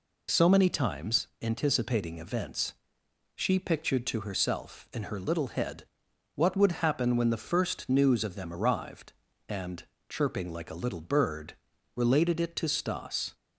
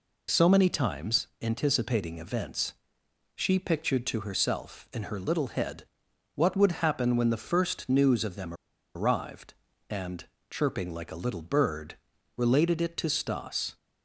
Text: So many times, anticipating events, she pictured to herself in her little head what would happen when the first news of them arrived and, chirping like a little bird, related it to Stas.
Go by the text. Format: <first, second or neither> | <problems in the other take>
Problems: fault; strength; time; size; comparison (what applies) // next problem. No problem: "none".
first | pauses between "head" and "what"; noticeable; at 5.8 s; 0.50 s long; noticeable in the first // pauses between "them" and "arrived"; at 8.5 s; 0.41 s long